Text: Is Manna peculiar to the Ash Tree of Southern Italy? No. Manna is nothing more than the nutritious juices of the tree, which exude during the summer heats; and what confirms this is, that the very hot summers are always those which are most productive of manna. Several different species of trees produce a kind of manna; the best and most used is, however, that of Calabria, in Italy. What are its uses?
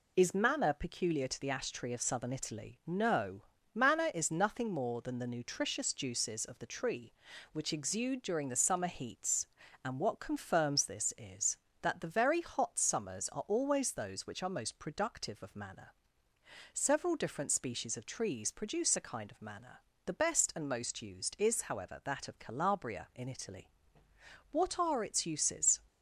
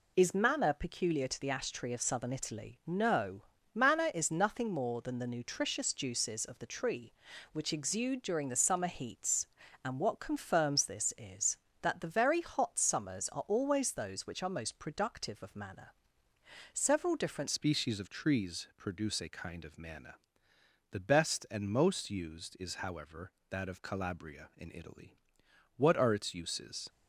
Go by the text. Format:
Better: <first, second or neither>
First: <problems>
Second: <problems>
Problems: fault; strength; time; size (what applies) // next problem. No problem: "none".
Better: first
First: none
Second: changes voice at "species"; from 17.4 s on; 9.4 s long